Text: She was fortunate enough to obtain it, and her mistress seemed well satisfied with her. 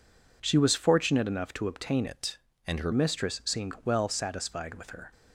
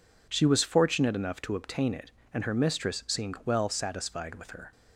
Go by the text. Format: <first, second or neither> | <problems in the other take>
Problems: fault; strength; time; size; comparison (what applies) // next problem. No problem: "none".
second | changes voice from "it" to "her"; from 2.0 to 2.8 s; 0.8 s long